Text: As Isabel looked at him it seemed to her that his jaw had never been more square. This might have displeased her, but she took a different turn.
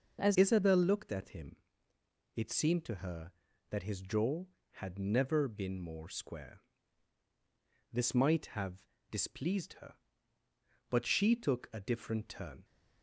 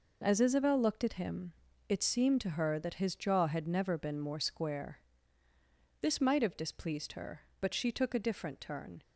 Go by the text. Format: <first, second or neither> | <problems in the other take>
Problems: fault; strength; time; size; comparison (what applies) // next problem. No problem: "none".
second | changes voice at "Isabel"; from 0.3 s on; 12.3 s long // pauses between "him" and "it"; noticeable; at 1.5 s; 0.78 s long; slight in the second // pauses between "have" and "displeased"; slight; at 8.8 s; 0.26 s long